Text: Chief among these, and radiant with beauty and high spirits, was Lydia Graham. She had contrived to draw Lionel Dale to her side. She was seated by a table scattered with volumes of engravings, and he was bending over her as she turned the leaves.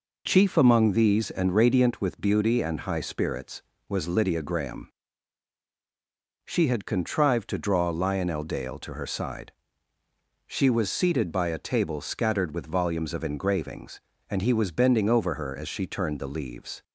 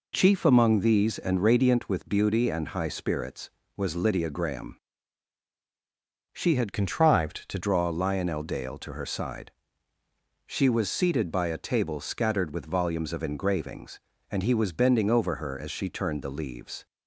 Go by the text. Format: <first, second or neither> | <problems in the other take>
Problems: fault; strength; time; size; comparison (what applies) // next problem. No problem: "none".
first | changes voice from "contrived" to "to"; from 6.7 to 7.5 s; 0.8 s long